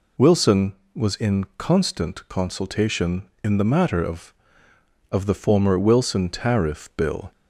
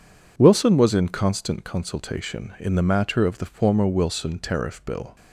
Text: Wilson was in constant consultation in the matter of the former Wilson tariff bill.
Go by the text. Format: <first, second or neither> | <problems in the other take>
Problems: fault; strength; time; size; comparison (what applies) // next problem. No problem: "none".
second | says "of" twice; at 5.0 s